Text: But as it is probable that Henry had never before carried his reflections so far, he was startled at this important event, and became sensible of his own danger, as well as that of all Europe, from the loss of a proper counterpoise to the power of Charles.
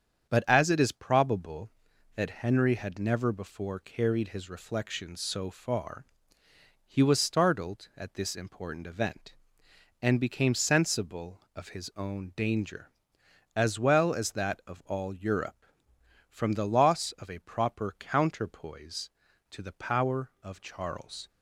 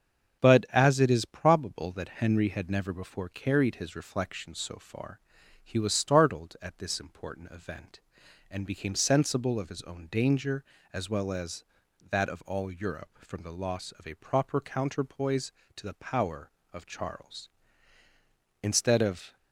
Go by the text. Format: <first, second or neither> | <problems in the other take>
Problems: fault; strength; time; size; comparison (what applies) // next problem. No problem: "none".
first | starts louder than the rest; until 1.4 s; 7 dB; strong in the first // goes on to say "Instead of"; noticeable; from 18.6 s on; 0.74 s long